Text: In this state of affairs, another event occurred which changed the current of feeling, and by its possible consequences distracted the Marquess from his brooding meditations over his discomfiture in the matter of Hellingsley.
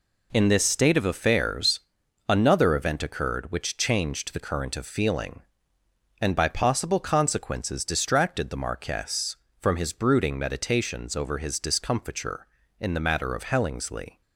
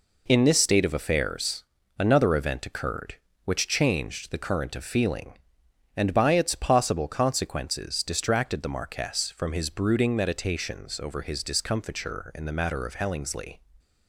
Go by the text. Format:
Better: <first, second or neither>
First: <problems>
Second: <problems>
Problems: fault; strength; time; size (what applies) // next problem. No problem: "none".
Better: second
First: skips "its"; at 6.4 s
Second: none